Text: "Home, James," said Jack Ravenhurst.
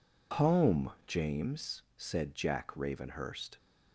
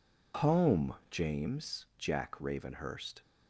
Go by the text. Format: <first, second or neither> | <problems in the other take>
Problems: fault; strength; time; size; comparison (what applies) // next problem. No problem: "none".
first | skips "said"; at 1.9 s